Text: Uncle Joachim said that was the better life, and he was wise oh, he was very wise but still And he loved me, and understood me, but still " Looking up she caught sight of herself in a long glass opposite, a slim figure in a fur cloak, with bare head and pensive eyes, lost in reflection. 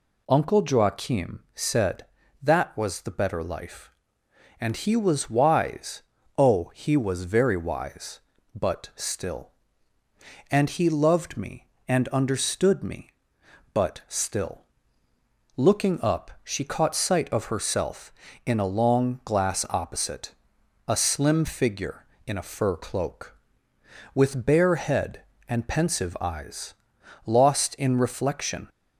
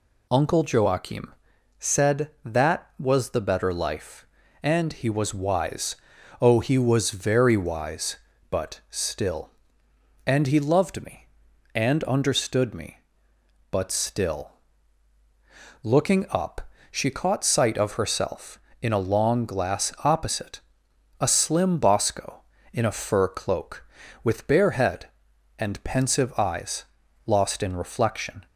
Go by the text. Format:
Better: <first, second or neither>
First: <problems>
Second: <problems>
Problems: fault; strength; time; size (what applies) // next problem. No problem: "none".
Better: first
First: pauses between "wise" and "oh"; slight; at 6.0 s; 0.36 s long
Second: pauses between "Joachim" and "said"; noticeable; at 1.3 s; 0.46 s long // pauses between "wise" and "oh"; at 5.9 s; 0.44 s long // pauses between "up" and "she"; slight; at 16.5 s; 0.32 s long // says "bosco" for "figure"; at 21.7 s